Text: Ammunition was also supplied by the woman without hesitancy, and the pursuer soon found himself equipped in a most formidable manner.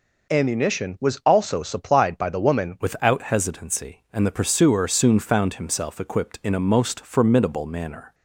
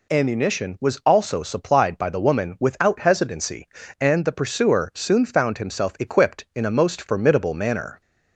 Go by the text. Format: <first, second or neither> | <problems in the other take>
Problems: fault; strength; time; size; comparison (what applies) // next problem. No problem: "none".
second | changes voice at "without"; from 2.7 s on; 5.4 s long